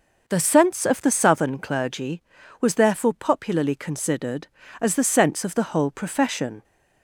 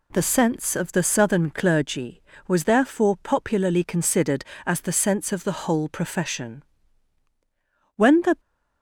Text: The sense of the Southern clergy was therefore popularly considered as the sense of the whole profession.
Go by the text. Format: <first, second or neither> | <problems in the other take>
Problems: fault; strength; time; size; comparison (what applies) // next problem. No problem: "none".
first | goes on to say "When the"; slight; from 7.9 s on; 0.44 s long